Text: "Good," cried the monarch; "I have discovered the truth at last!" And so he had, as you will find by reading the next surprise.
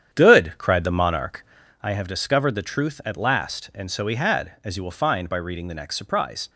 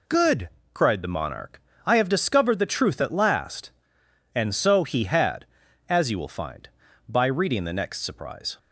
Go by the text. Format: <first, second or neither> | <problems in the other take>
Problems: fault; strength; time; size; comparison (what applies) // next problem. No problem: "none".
second | starts louder than the rest; strong; until 1.8 s; 9 dB